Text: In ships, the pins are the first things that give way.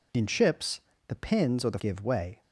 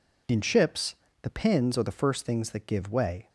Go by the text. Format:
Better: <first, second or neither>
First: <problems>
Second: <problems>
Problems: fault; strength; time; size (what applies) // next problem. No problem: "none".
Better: second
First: skips "first things that"; at 1.7 s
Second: none